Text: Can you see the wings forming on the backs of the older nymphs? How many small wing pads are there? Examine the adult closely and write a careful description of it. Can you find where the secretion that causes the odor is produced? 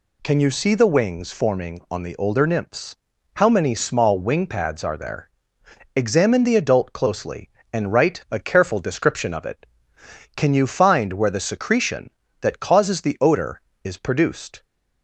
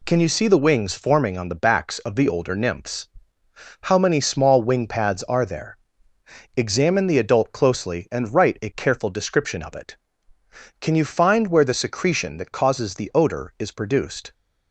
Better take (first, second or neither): second